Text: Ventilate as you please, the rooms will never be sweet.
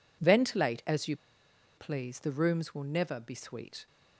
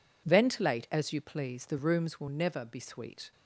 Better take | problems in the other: second | pauses between "you" and "please"; noticeable; at 1.1 s; 0.61 s long

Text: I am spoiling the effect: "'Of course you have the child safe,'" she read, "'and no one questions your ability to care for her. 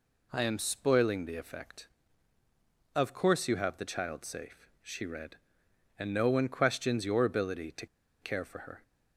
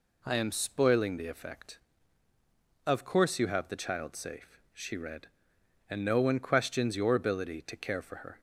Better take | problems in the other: second | pauses between "to" and "care"; slight; at 7.8 s; 0.35 s long

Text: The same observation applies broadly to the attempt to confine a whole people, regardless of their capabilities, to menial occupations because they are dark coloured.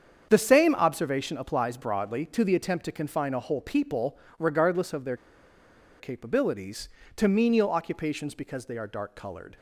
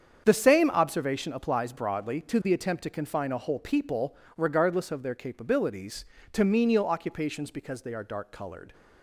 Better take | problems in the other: second | starts louder than the rest; strong; until 1.3 s; 7.5 dB; strong in the second // pauses between "their" and "capabilities"; noticeable; at 5.1 s; 0.83 s long

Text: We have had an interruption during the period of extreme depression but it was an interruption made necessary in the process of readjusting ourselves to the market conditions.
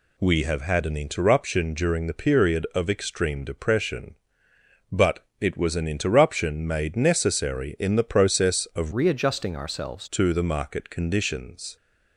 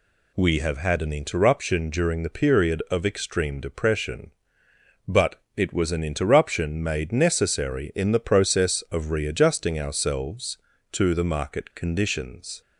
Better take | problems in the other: second | pauses between "but" and "it"; slight; at 5.2 s; 0.16 s long; slight in the second // changes voice from "readjusting" to "ourselves"; from 8.9 to 10.0 s; 1.1 s long

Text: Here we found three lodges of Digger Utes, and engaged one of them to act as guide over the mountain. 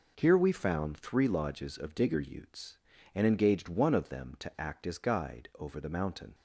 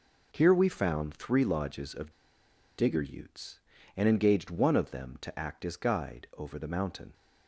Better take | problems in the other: first | pauses between "of" and "Digger"; noticeable; at 2.0 s; 0.67 s long

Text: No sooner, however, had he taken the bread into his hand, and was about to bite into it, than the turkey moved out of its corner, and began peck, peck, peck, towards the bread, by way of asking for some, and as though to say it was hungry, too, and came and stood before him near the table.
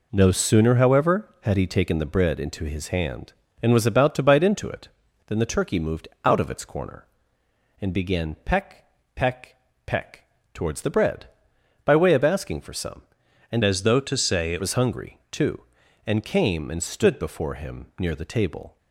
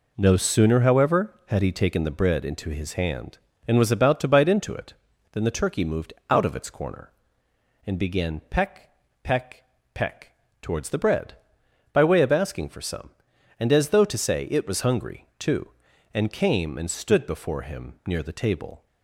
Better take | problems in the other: second | pauses between "moved" and "out"; slight; at 6.0 s; 0.16 s long; slight in the second // changes voice from "as" to "it"; from 13.6 to 14.6 s; 1.0 s long

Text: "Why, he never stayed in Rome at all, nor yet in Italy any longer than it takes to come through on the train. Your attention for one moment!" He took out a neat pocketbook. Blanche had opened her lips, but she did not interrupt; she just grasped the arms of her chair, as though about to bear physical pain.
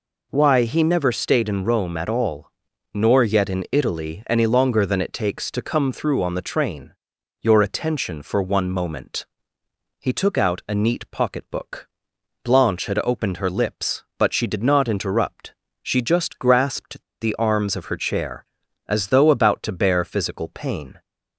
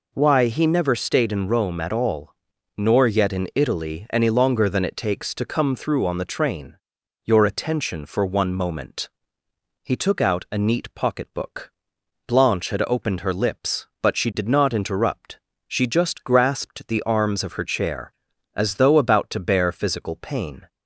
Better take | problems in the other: second | pauses between "grasped" and "the"; slight; at 17.0 s; 0.19 s long

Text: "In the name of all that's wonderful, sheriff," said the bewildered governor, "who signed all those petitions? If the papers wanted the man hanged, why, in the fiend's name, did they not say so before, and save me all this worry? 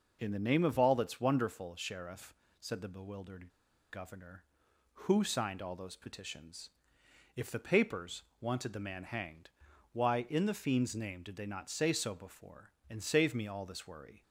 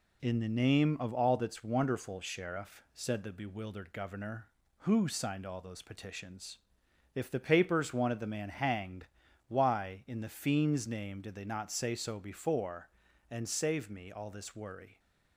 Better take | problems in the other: second | pauses between "bewildered" and "governor"; at 3.4 s; 0.44 s long // pauses between "papers" and "wanted"; slight; at 8.2 s; 0.18 s long

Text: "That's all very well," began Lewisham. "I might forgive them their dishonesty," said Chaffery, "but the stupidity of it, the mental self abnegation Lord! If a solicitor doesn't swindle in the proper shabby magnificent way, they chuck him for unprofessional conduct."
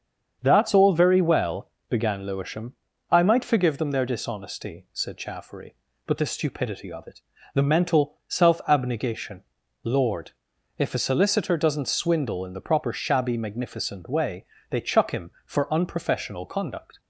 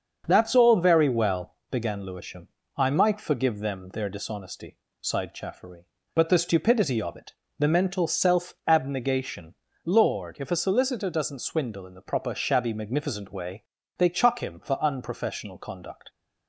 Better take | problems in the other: first | starts louder than the rest; until 1.2 s; 7 dB; also in the first // says "sighed" for "said"; at 4.9 s // pauses between "abnegation" and "Lord"; slight; at 9.5 s; 0.32 s long; also in the first

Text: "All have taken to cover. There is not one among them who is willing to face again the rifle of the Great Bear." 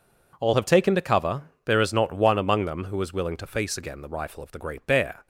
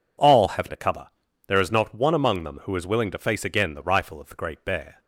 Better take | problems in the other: first | skips "taken"; at 0.6 s

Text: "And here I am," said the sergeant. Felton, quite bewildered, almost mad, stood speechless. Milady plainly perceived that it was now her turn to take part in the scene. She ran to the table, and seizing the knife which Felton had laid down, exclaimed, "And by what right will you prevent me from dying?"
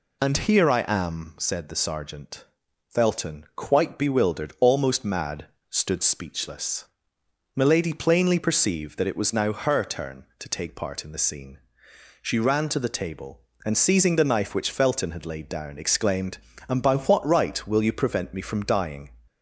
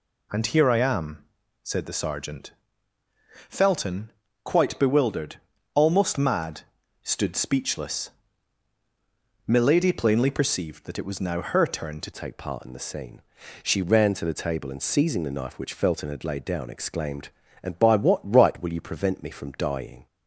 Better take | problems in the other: first | changes voice at "take"; from 12.1 s on; 7.9 s long

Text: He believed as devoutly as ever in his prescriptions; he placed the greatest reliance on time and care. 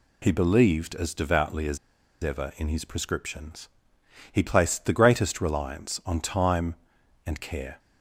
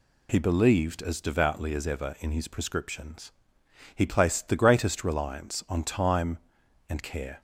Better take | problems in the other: second | pauses between "as" and "ever"; noticeable; at 1.7 s; 0.46 s long

